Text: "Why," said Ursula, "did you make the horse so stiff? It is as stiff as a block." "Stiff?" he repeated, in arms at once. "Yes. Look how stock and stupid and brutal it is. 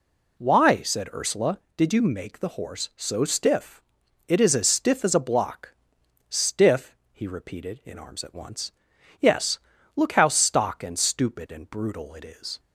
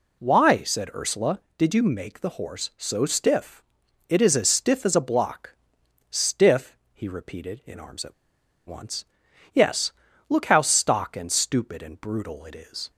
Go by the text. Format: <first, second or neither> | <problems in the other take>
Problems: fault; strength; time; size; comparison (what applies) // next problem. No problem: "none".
first | pauses between "at" and "once"; noticeable; at 8.1 s; 0.53 s long